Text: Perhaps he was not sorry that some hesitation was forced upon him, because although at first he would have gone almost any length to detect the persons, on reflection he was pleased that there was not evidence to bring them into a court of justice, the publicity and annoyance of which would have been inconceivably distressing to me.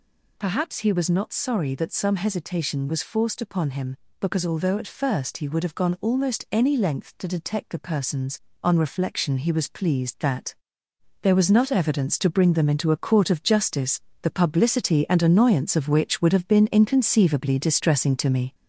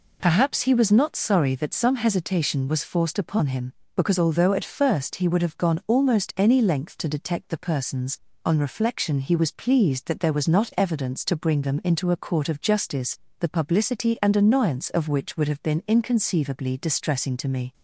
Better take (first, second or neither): second